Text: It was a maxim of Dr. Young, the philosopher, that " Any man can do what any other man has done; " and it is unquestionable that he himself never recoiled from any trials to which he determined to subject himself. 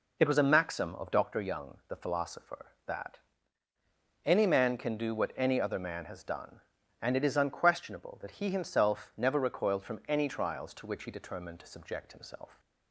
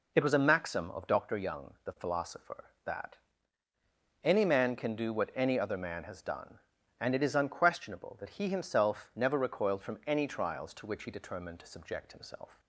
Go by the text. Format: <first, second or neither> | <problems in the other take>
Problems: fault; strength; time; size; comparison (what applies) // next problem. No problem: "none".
neither | none